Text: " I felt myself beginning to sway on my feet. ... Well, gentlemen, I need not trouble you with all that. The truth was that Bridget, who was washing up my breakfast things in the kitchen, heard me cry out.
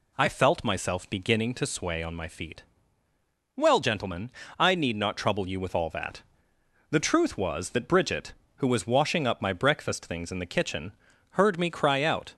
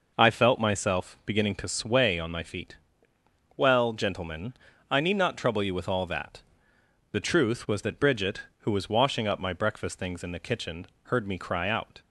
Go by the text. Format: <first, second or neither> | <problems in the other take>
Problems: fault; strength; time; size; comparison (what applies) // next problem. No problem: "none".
neither | none